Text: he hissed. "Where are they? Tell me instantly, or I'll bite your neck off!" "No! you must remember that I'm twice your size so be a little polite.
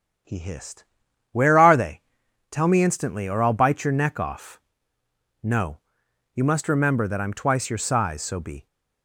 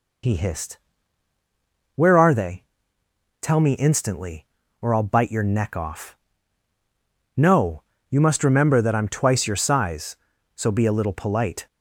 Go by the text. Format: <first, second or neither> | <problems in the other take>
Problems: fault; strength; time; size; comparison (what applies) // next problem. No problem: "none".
second | starts louder than the rest; strong; until 1.7 s; 8.5 dB // stops before "a little polite"; at 8.6 s